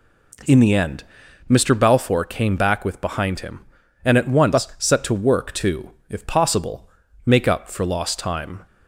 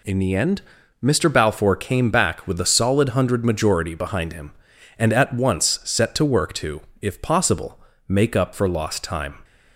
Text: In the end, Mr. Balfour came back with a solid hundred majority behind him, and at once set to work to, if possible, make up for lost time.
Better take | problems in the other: second | skips "a solid hundred majority"; at 2.9 s

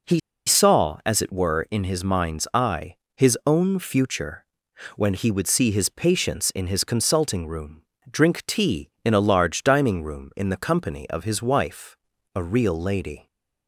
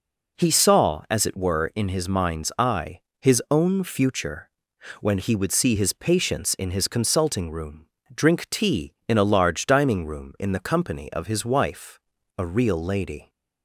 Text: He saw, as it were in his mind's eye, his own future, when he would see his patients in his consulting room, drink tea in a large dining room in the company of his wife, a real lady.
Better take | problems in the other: second | pauses between "He" and "saw"; slight; at 0.1 s; 0.26 s long

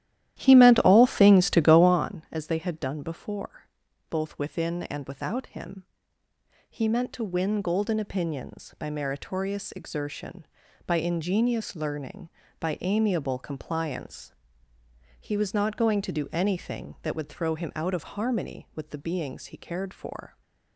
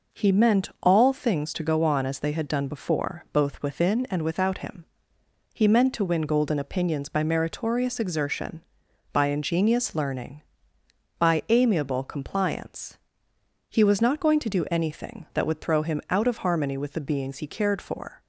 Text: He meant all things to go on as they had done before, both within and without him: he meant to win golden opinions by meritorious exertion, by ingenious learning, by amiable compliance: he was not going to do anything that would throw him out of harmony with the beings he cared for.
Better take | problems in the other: second | starts louder than the rest; strong; until 2.1 s; 12.5 dB

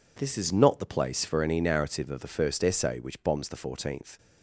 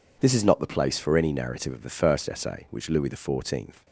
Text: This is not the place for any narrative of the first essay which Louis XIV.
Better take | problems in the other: second | says "Bombs" for "Louis"; at 3.2 s

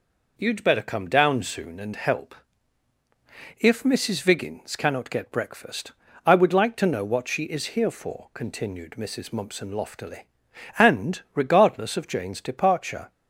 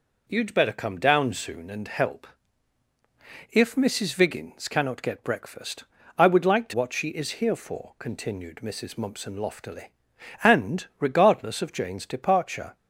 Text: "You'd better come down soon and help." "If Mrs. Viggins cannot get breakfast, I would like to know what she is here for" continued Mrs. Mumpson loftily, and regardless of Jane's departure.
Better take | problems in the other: first | skips "know"; at 6.7 s

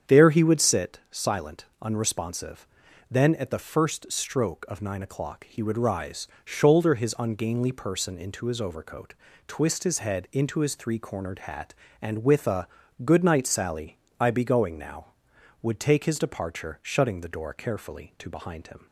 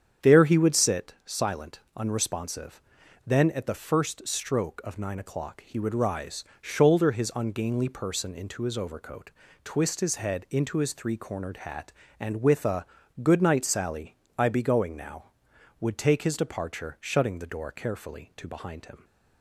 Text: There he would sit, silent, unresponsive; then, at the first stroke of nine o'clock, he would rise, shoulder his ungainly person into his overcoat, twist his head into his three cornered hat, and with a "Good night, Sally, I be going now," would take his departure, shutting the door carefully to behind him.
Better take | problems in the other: neither | starts louder than the rest; strong; the same in both // pauses between "a" and "Good"; slight; the same in both

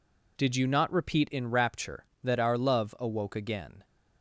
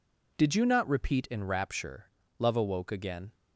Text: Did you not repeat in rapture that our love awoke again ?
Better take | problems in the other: first | skips "that our"; at 2.2 s

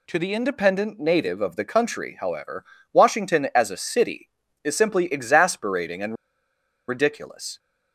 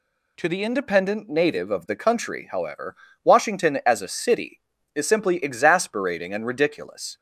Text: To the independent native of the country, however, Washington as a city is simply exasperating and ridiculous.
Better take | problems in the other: second | pauses between "and" and "ridiculous"; noticeable; at 6.1 s; 0.74 s long

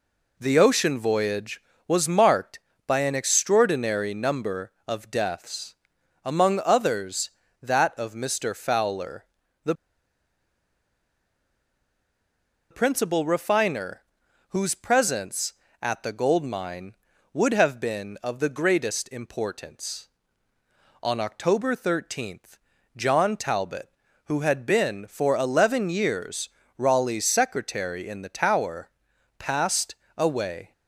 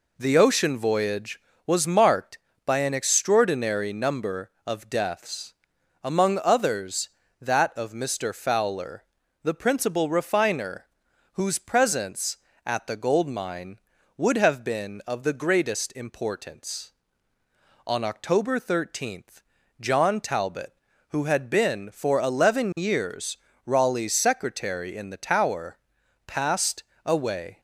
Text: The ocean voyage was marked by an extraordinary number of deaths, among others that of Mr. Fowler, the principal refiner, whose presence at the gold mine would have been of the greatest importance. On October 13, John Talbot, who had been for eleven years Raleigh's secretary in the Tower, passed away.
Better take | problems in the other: second | pauses between "the" and "principal"; strong; at 9.7 s; 2.9 s long // pauses between "years" and "Raleigh's"; slight; at 26.4 s; 0.26 s long; slight in the second // pauses between "passed" and "away"; slight; at 29.9 s; 0.22 s long; slight in the second

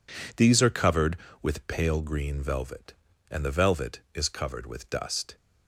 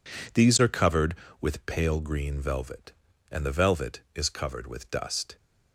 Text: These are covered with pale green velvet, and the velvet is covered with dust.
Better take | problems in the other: neither | none

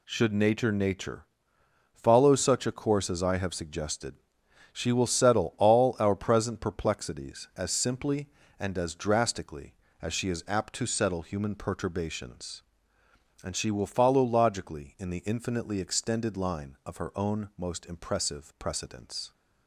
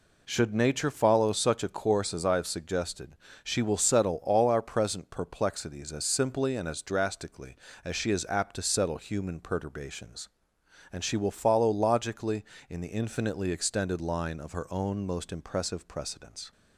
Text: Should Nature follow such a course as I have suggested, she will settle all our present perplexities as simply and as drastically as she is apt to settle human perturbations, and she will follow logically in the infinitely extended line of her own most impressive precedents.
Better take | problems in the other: second | says "Nature" twice; at 0.7 s

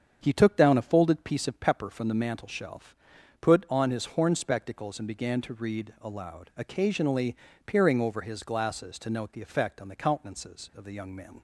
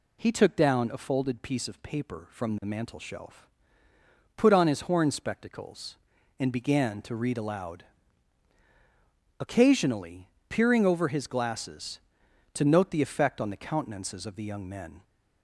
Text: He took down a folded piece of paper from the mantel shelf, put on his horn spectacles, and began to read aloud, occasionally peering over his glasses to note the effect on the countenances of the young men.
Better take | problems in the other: second | starts louder than the rest; strong; until 1.2 s; 7.5 dB // says "pepper" for "paper"; at 1.5 s // pauses between "occasionally" and "peering"; slight; at 7.3 s; 0.32 s long; slight in the second

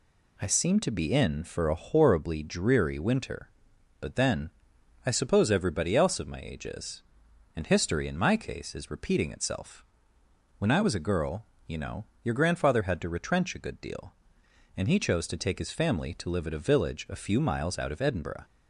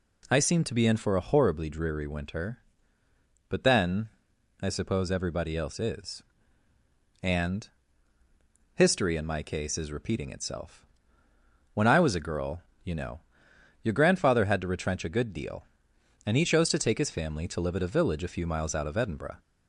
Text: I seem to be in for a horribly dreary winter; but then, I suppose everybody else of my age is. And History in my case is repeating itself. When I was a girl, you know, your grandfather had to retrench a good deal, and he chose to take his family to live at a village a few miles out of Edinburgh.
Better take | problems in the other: first | skips "of my age"; at 5.7 s // pauses between "And" and "History"; at 7.6 s; 1.0 s long

